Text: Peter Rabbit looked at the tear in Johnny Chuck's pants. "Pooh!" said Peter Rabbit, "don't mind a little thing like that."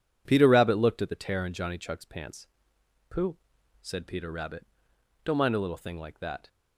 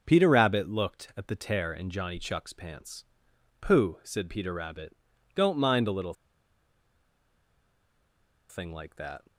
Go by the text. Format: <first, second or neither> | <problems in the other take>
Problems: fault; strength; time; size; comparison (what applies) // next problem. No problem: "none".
first | pauses between "little" and "thing"; strong; at 6.1 s; 2.3 s long